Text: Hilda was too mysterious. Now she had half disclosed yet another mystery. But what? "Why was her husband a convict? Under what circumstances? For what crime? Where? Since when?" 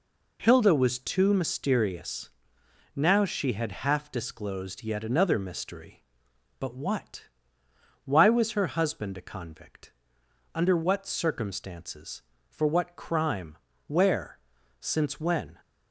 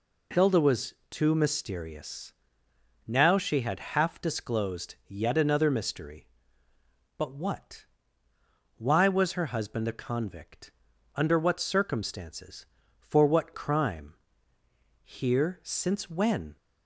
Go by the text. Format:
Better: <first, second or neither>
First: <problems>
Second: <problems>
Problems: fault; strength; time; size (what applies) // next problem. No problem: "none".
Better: first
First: none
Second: pauses between "was" and "too"; slight; at 0.9 s; 0.16 s long // says "Here" for "Where"; at 15.0 s